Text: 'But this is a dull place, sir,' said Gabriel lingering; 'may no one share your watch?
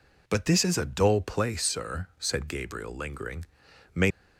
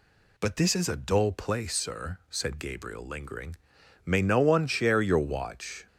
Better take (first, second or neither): second